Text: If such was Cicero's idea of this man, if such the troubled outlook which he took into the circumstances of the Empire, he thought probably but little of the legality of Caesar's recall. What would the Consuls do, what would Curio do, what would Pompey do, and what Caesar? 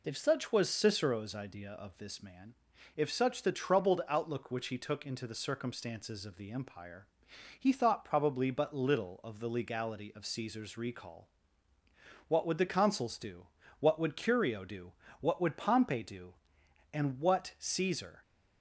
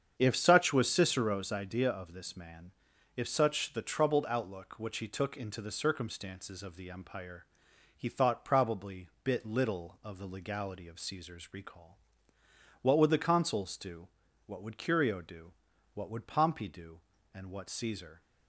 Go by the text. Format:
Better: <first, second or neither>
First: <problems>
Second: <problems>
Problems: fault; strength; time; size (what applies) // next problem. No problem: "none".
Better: first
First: none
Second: starts louder than the rest; strong; until 1.1 s; 7.5 dB // says "bit" for "but"; at 9.2 s